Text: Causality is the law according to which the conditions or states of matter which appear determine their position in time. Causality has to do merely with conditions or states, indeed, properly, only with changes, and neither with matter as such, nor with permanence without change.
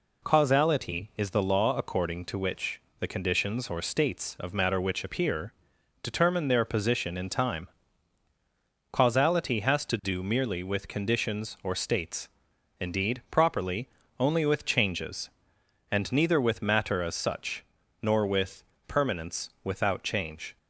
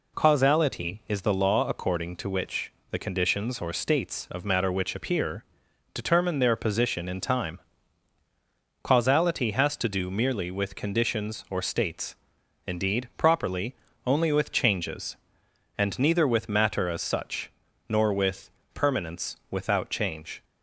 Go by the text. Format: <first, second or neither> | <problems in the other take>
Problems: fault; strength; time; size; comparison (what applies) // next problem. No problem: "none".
neither | pauses between "which" and "the"; slight; the same in both // pauses between "appear" and "determine"; noticeable; the same in both // pauses between "with" and "permanence"; slight; the same in both